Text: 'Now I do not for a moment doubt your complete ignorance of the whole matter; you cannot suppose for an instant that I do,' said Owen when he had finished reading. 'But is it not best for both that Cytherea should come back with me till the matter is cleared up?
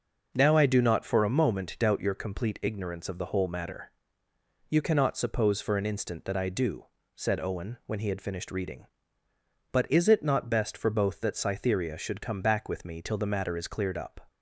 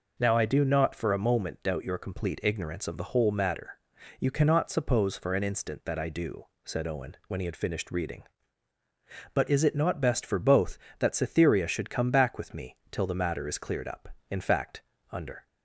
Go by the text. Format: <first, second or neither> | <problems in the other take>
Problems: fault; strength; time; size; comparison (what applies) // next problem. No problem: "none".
first | pauses between "me" and "till"; slight; at 12.7 s; 0.16 s long // goes on to say "In fact under"; noticeable; from 14.3 s on; 1.1 s long